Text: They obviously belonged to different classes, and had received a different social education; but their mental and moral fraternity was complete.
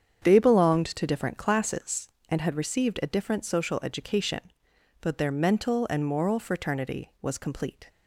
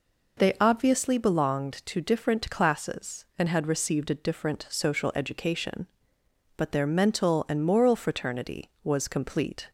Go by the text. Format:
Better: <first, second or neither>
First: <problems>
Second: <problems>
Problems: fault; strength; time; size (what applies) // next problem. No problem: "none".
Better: second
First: starts louder than the rest; strong; until 1.2 s; 7.5 dB // skips "obviously"; at 0.3 s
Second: none